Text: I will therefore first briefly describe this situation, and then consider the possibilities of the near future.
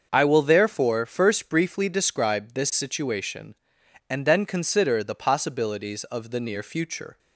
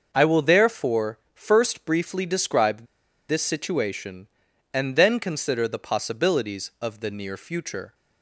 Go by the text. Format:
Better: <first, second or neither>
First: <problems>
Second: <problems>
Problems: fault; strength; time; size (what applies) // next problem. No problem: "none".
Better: first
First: starts louder than the rest; until 1.1 s; 6.5 dB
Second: starts louder than the rest; until 1.1 s; 6 dB // pauses between "therefore" and "first"; slight; at 1.1 s; 0.16 s long // pauses between "describe" and "this"; at 2.8 s; 0.45 s long